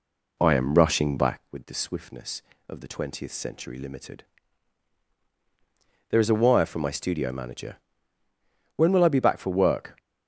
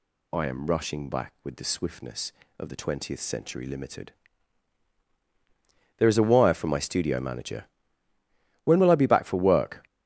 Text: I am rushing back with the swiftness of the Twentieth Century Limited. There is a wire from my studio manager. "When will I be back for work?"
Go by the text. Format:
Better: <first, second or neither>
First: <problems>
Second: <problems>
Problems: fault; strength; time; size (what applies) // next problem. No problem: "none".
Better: second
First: starts louder than the rest; slight; until 1.5 s; 2.5 dB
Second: none